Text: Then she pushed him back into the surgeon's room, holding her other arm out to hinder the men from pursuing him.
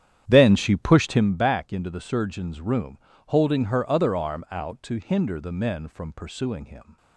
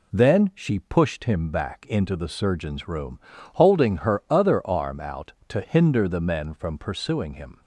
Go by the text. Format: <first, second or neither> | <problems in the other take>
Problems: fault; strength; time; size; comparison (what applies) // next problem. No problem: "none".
second | starts louder than the rest; strong; until 1.3 s; 10 dB